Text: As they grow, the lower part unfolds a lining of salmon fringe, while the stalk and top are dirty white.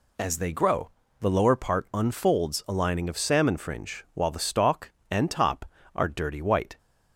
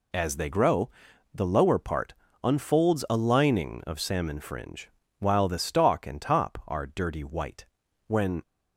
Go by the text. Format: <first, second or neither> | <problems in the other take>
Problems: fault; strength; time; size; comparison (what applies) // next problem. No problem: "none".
first | pauses between "part" and "unfolds"; slight; at 2.1 s; 0.28 s long // goes on to say "When"; slight; from 8.0 s on; 0.34 s long